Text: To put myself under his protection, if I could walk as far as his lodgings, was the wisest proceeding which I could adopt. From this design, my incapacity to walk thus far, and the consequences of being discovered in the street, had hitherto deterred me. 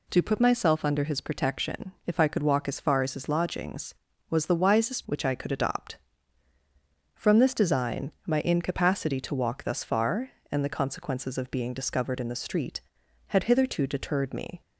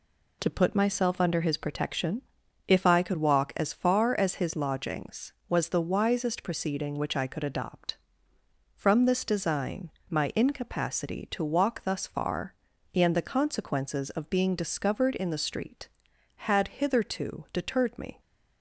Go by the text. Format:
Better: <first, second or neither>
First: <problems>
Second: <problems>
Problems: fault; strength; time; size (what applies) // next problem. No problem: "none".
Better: second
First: skips "proceeding"; at 5.0 s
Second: none